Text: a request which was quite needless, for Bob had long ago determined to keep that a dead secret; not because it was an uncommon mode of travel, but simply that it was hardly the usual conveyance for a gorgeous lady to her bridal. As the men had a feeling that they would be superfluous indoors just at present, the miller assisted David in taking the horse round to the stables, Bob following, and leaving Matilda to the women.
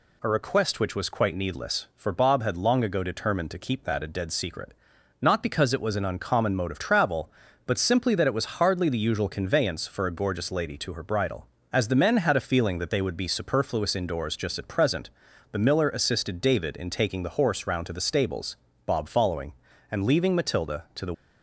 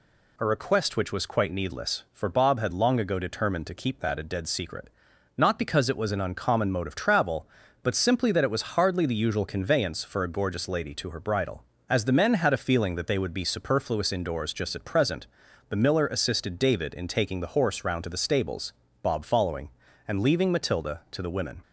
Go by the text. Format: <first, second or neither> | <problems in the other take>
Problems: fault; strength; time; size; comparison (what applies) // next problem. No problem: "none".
second | stops before "women"; at 21.1 s